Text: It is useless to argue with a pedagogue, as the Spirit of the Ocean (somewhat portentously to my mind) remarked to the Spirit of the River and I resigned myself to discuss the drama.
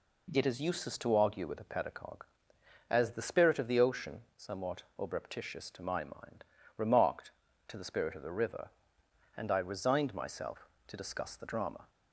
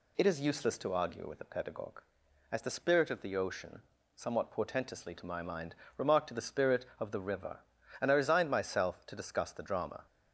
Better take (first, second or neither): second